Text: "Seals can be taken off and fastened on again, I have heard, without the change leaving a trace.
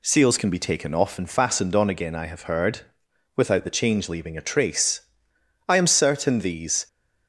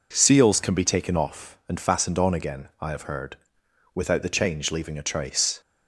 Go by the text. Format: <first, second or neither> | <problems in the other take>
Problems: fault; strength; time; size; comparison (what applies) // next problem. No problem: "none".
second | goes on to say "I am certain these"; noticeable; from 5.6 s on; 1.2 s long